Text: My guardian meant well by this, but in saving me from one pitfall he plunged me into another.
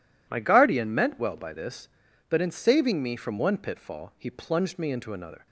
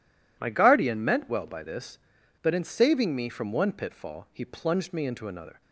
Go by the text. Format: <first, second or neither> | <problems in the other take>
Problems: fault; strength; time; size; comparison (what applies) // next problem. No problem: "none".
neither | none